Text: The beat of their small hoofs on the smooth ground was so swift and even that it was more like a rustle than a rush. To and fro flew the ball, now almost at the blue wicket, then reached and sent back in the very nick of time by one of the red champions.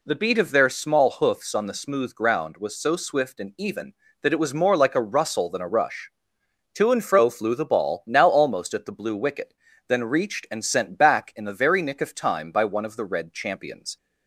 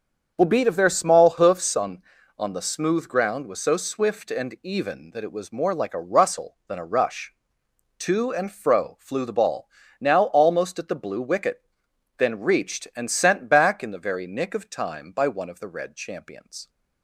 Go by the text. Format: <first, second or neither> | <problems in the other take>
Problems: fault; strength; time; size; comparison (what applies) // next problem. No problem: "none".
first | starts louder than the rest; until 1.3 s; 6.5 dB // says "on" twice; at 2.3 s